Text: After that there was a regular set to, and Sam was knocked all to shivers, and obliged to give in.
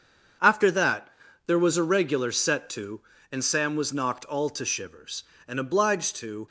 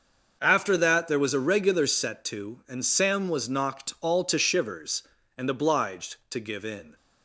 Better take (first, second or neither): second